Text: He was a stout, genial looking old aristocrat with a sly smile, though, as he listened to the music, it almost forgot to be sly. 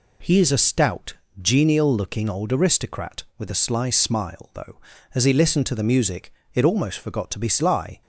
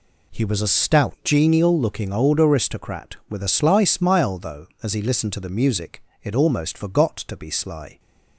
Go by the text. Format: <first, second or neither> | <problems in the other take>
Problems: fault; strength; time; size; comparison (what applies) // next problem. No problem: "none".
second | says "is" for "was"; at 0.3 s